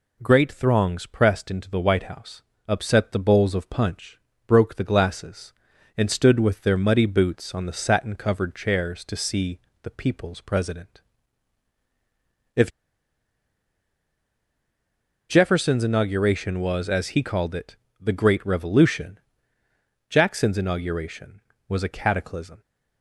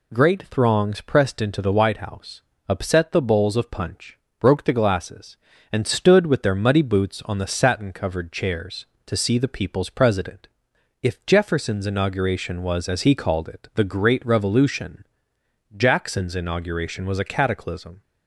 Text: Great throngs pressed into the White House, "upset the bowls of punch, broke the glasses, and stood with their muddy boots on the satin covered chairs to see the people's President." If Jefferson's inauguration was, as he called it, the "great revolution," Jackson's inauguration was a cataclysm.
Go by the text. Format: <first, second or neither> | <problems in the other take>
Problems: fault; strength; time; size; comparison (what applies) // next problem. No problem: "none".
second | pauses between "see" and "the"; slight; at 9.5 s; 0.24 s long // pauses between "If" and "Jefferson's"; strong; at 12.6 s; 2.5 s long